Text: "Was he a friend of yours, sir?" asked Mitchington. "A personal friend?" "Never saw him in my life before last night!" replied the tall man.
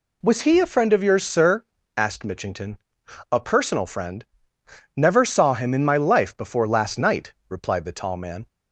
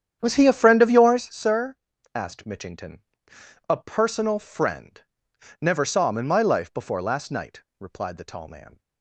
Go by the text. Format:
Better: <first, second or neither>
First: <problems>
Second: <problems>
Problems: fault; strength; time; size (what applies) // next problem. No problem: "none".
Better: first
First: none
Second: starts louder than the rest; strong; until 1.3 s; 9 dB